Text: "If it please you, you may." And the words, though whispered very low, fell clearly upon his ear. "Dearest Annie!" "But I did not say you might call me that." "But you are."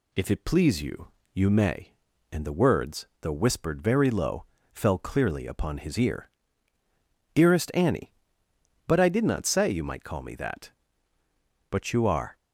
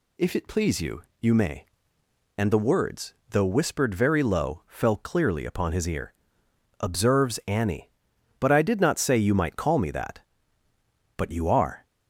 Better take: first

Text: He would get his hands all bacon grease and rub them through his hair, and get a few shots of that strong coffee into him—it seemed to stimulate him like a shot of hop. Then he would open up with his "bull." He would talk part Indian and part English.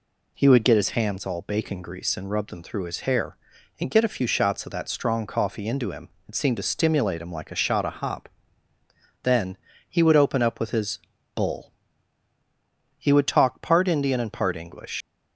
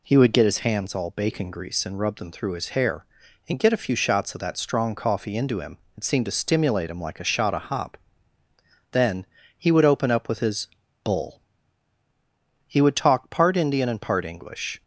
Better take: second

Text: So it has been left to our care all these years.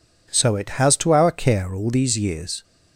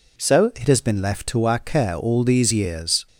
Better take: second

